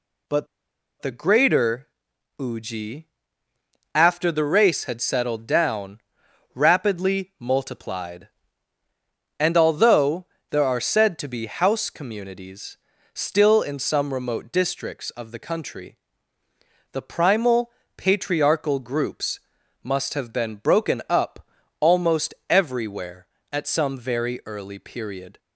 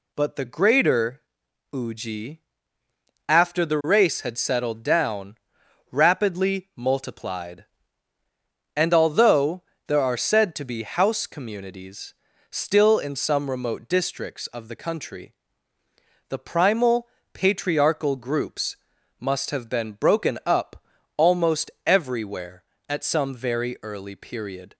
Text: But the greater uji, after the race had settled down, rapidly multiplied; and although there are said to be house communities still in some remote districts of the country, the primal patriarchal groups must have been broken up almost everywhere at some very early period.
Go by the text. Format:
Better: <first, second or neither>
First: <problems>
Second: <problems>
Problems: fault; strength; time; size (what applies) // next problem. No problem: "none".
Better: second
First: pauses between "But" and "the"; noticeable; at 0.4 s; 0.55 s long // pauses between "greater" and "uji"; noticeable; at 1.8 s; 0.50 s long // pauses between "although" and "there"; slight; at 10.2 s; 0.24 s long // pauses between "communities" and "still"; slight; at 12.7 s; 0.36 s long // pauses between "primal" and "patriarchal"; slight; at 17.7 s; 0.26 s long // pauses between "groups" and "must"; at 19.4 s; 0.42 s long // pauses between "up" and "almost"; slight; at 21.4 s; 0.36 s long // pauses between "almost" and "everywhere"; slight; at 22.3 s; 0.16 s long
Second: pauses between "greater" and "uji"; noticeable; at 1.2 s; 0.50 s long // pauses between "although" and "there"; slight; at 9.6 s; 0.24 s long // pauses between "communities" and "still"; slight; at 12.1 s; 0.36 s long // pauses between "primal" and "patriarchal"; slight; at 17.0 s; 0.26 s long // pauses between "groups" and "must"; at 18.7 s; 0.42 s long // pauses between "up" and "almost"; slight; at 20.8 s; 0.36 s long // pauses between "almost" and "everywhere"; slight; at 21.6 s; 0.16 s long